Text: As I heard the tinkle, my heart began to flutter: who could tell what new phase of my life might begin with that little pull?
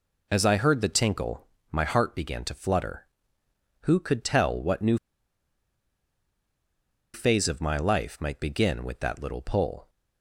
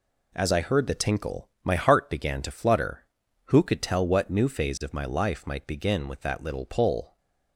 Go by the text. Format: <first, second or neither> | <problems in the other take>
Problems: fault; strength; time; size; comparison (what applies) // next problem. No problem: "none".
second | pauses between "new" and "phase"; strong; at 4.9 s; 2.1 s long